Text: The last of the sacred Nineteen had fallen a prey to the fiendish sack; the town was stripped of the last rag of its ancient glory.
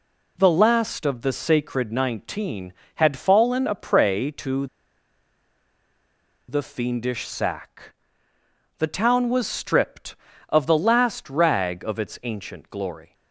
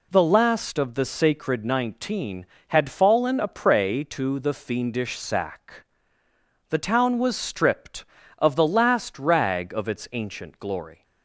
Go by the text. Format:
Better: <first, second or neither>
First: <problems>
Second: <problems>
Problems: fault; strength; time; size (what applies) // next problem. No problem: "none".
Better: second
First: pauses between "to" and "the"; strong; at 4.6 s; 1.8 s long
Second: none